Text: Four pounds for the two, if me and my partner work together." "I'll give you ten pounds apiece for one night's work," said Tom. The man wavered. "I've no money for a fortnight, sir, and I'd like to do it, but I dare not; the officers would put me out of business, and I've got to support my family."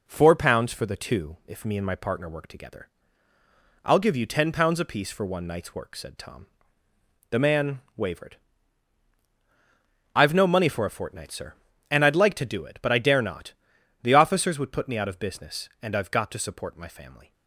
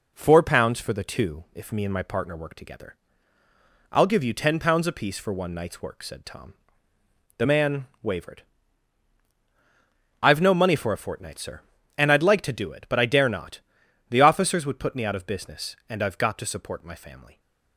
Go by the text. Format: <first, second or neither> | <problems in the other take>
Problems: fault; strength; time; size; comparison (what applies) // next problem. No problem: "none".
neither | pauses between "man" and "wavered"; slight; the same in both